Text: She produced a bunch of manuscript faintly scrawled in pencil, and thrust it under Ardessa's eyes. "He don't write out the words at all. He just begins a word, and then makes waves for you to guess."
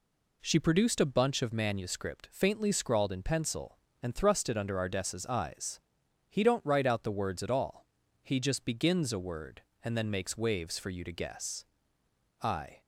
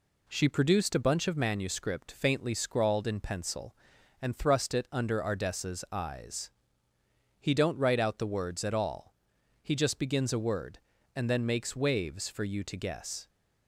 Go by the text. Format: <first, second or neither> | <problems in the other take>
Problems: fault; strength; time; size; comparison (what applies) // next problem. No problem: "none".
second | goes on to say "I"; slight; from 12.4 s on; 0.40 s long